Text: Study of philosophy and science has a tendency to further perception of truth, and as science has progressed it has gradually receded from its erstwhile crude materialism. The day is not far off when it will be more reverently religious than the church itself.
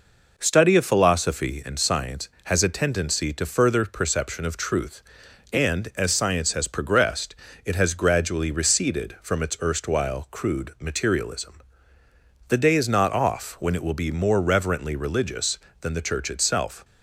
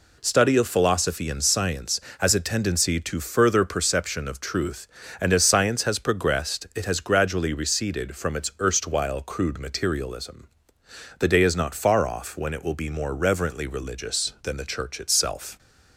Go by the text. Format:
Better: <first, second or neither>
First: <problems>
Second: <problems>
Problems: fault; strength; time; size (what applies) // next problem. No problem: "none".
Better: second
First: pauses between "progressed" and "it"; slight; at 7.3 s; 0.30 s long // skips "far"; at 13.1 s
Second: none